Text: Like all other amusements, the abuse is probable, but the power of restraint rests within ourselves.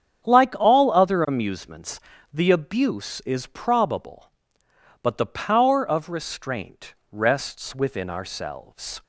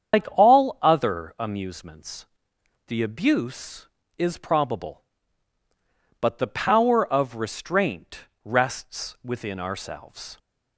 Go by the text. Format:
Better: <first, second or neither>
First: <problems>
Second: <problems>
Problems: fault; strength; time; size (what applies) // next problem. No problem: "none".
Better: first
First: starts louder than the rest; strong; until 1.3 s; 8.5 dB // pauses between "restraint" and "rests"; slight; at 6.9 s; 0.16 s long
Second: loses the start of "Like"; at 0.1 s; 125 ms // starts louder than the rest; strong; until 1.2 s; 7.5 dB // pauses between "restraint" and "rests"; slight; at 8.1 s; 0.24 s long